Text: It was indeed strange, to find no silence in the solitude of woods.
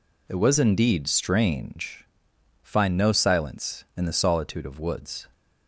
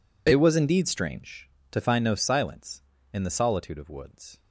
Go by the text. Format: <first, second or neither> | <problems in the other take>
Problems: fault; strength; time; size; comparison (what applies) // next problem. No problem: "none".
second | skips "to"; at 2.3 s